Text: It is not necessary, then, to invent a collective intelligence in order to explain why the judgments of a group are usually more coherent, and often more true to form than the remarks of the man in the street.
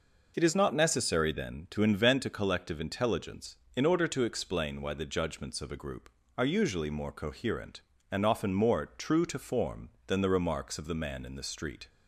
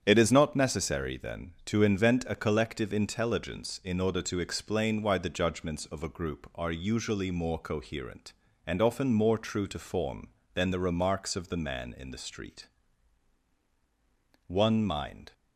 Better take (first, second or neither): first